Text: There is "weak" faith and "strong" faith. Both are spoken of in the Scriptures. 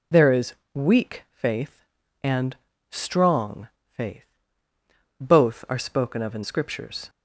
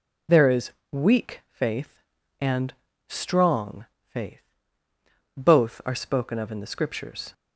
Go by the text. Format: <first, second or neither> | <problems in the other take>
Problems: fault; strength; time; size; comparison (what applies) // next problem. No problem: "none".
second | pauses between "is" and "weak"; slight; at 0.5 s; 0.22 s long; slight in the second // pauses between "and" and "strong"; slight; at 2.5 s; 0.34 s long; slight in the second // pauses between "strong" and "faith"; slight; at 3.6 s; 0.22 s long; slight in the second // skips "the"; at 6.4 s